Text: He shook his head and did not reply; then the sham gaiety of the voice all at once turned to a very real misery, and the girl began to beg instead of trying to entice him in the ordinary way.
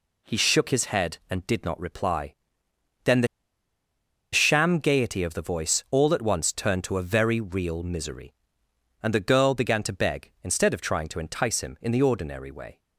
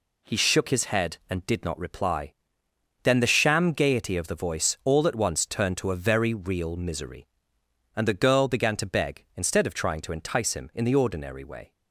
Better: second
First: pauses between "the" and "sham"; at 3.2 s; 1.0 s long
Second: none

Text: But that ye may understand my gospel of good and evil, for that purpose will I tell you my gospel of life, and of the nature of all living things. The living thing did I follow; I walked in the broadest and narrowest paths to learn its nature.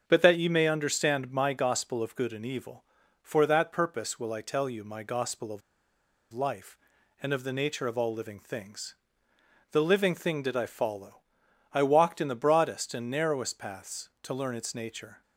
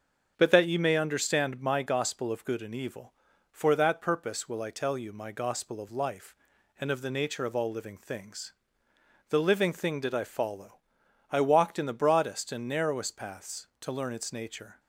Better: second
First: starts louder than the rest; until 1.0 s; 7 dB // pauses between "of" and "life"; noticeable; at 5.6 s; 0.72 s long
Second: starts louder than the rest; until 1.3 s; 7 dB

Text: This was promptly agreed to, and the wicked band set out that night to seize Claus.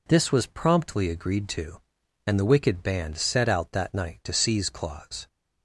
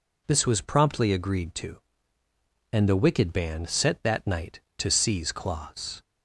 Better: first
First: none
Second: skips "out"; at 4.0 s

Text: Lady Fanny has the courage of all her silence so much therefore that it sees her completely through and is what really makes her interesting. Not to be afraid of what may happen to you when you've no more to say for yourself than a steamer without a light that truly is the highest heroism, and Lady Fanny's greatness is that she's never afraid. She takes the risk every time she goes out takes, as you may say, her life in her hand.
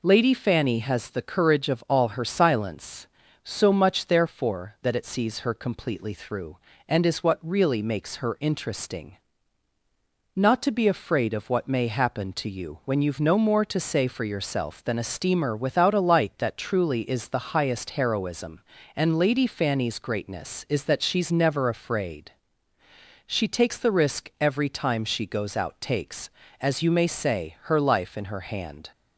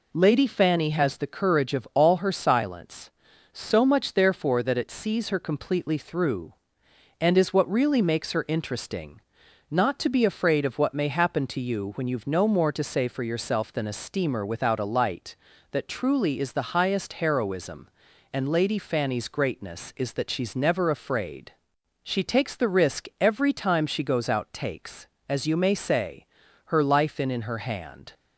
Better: first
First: none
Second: says "in" twice; at 27.2 s

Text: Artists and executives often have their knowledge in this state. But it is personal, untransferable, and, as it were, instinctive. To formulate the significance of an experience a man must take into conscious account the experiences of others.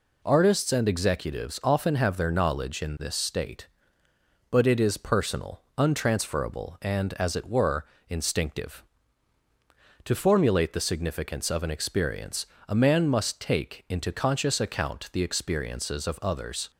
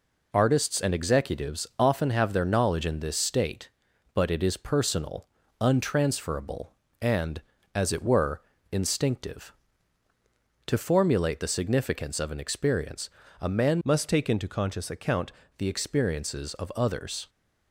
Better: first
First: pauses between "experience" and "a"; slight; at 12.4 s; 0.22 s long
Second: pauses between "experience" and "a"; slight; at 13.0 s; 0.32 s long // changes voice from "must" to "account"; from 13.8 to 15.3 s; 1.5 s long

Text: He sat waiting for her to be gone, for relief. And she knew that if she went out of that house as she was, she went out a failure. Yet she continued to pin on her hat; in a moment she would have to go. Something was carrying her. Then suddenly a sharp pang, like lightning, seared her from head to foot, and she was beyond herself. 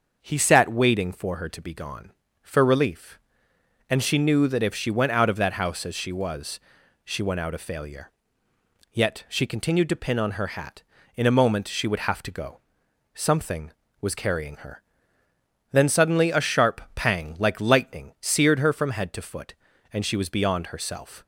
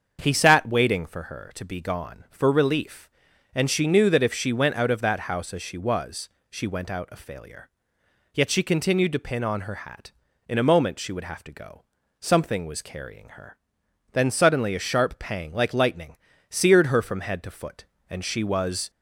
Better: first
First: starts louder than the rest; until 1.2 s; 6.5 dB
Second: starts louder than the rest; until 1.2 s; 7 dB // stops before "beyond herself"; at 18.8 s

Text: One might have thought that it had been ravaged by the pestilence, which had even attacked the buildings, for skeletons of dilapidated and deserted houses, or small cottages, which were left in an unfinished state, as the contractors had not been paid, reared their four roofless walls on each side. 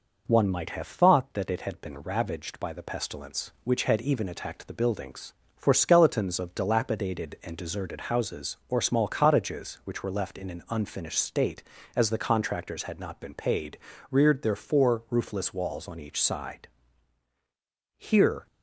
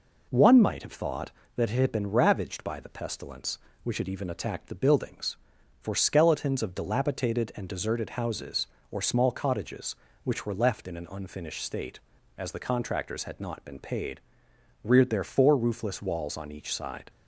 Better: second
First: goes on to say "Here"; from 17.9 s on; 0.50 s long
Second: none

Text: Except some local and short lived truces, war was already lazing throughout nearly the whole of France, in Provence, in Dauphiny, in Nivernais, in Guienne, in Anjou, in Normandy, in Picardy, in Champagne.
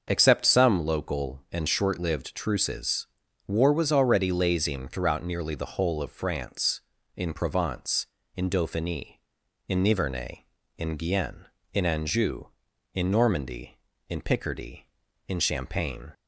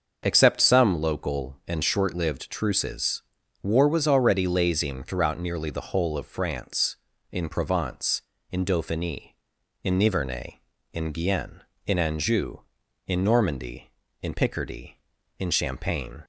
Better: neither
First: starts louder than the rest; until 1.1 s; 6.5 dB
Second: starts louder than the rest; until 1.2 s; 6.5 dB

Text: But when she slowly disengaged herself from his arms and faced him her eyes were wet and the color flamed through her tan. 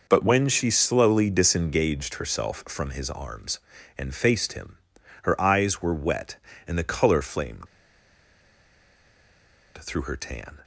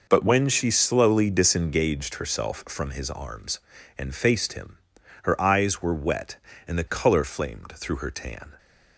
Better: second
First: pauses between "him" and "her"; noticeable; at 4.7 s; 0.46 s long // pauses between "flamed" and "through"; strong; at 7.6 s; 2.1 s long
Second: pauses between "him" and "her"; noticeable; at 4.7 s; 0.46 s long

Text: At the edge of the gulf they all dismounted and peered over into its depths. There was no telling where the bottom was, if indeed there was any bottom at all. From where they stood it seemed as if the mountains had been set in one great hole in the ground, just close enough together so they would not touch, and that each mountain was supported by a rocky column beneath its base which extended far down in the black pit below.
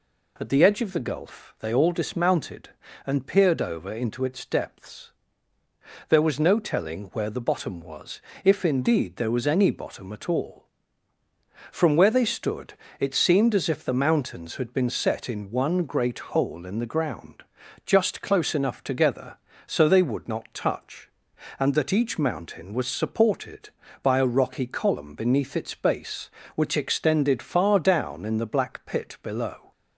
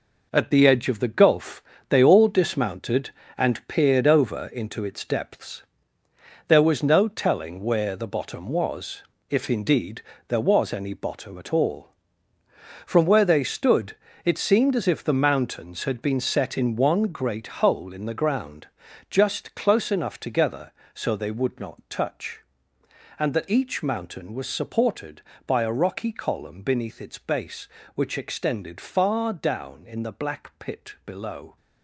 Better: first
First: pauses between "stood" and "it"; slight; at 12.7 s; 0.24 s long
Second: gets quieter; strong; throughout; 8.5 dB // pauses between "gulf" and "they"; slight; at 1.6 s; 0.26 s long // pauses between "indeed" and "there"; slight; at 10.0 s; 0.24 s long // pauses between "stood" and "it"; slight; at 13.9 s; 0.30 s long

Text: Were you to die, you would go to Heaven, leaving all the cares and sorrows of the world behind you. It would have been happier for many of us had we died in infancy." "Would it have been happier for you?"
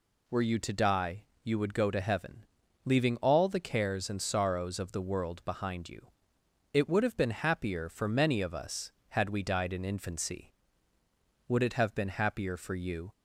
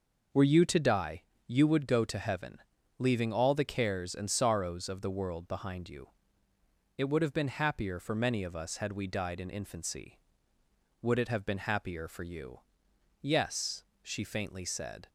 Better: first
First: none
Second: goes on to say "Yes she faintly said"; strong; from 13.2 s on; 1.8 s long

